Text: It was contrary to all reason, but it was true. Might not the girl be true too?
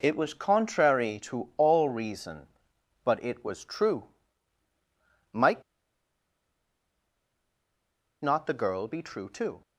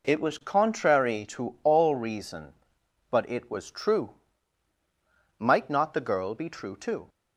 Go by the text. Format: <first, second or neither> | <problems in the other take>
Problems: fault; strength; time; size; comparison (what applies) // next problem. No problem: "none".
second | pauses between "Might" and "not"; strong; at 5.6 s; 2.5 s long